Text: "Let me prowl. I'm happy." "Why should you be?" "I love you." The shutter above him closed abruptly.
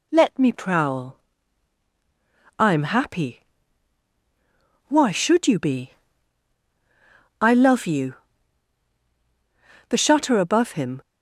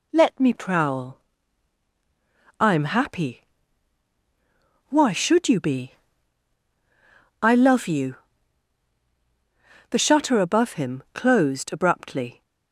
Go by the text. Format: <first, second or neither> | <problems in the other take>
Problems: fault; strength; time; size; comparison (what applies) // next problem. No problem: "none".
second | stops before "closed abruptly"; at 11.0 s